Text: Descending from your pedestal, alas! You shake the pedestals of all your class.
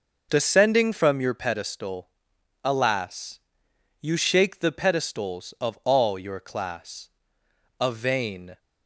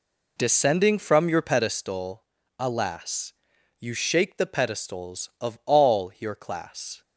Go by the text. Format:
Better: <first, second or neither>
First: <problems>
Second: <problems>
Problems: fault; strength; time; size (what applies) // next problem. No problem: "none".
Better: second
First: goes on to say "A vain"; noticeable; from 7.8 s on; 0.78 s long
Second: none